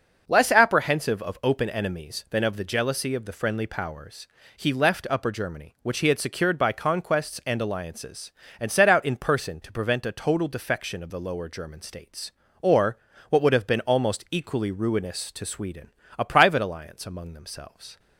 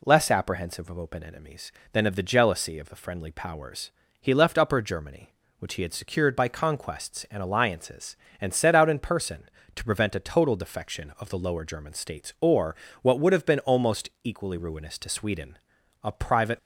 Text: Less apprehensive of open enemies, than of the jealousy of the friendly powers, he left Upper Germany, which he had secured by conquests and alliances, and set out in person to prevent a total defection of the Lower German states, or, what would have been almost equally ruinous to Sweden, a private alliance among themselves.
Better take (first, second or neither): first